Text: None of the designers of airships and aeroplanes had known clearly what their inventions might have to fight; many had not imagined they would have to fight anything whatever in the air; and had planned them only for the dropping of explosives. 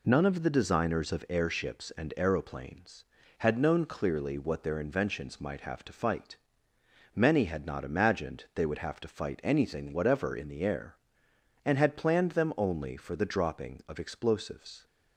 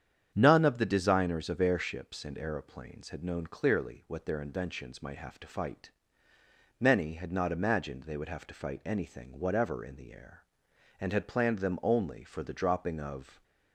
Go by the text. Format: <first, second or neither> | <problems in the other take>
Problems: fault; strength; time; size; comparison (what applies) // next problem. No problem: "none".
first | starts louder than the rest; strong; until 1.3 s; 8.5 dB // stops before "explosives"; at 13.4 s